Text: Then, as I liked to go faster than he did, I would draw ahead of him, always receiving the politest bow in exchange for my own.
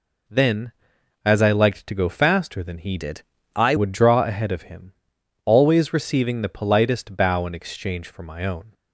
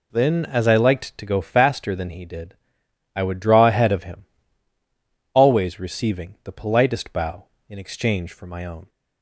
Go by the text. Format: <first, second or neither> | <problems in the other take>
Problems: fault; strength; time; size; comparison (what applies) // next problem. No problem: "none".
second | changes voice from "did" to "I"; from 2.9 to 3.7 s; 0.8 s long